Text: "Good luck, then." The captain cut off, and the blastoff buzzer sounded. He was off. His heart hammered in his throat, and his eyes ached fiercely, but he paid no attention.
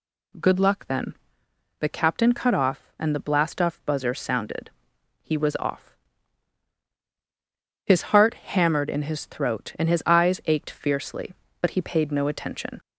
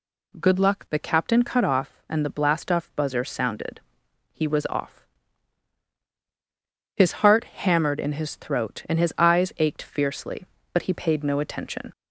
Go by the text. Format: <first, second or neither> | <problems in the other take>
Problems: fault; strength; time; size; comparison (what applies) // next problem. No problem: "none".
first | skips "then"; at 0.8 s